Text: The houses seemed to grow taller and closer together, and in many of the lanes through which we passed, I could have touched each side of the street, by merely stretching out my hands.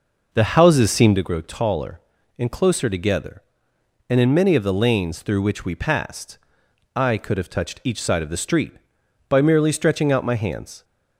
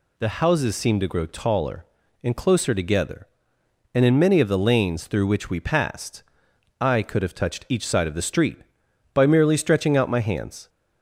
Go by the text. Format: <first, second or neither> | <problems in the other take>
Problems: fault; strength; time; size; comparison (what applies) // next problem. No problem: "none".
second | starts louder than the rest; noticeable; until 1.2 s; 5 dB